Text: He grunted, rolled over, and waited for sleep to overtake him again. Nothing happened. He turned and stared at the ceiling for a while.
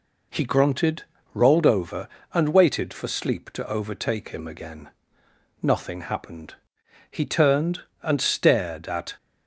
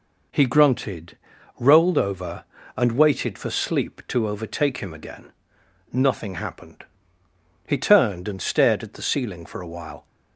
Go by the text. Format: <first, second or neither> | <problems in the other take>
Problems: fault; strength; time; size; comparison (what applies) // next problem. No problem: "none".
second | stops before "the ceiling for a while"; at 9.1 s